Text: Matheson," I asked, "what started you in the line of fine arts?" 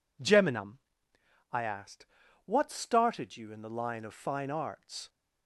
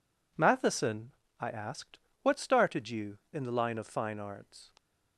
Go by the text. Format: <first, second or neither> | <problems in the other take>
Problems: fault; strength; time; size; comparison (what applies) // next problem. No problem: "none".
second | says "Geminum" for "Matheson"; at 0.2 s